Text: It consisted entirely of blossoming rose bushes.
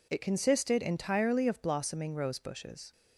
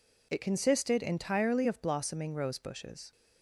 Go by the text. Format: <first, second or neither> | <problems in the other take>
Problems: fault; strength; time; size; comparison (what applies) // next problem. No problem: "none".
neither | none